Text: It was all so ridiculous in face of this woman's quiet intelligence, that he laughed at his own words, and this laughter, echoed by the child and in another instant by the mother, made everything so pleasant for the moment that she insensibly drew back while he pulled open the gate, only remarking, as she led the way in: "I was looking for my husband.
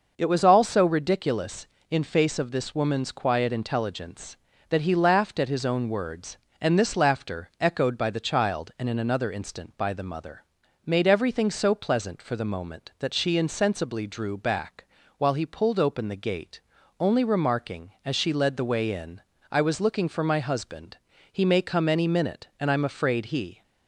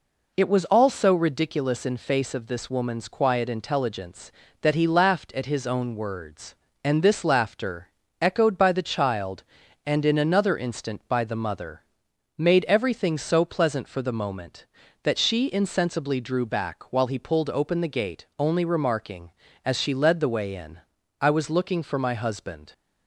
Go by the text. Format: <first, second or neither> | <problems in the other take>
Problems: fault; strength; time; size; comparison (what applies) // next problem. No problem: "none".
second | pauses between "back" and "while"; slight; at 14.8 s; 0.32 s long // goes on to say "He may come any minute and I'm afraid he"; strong; from 21.2 s on; 2.3 s long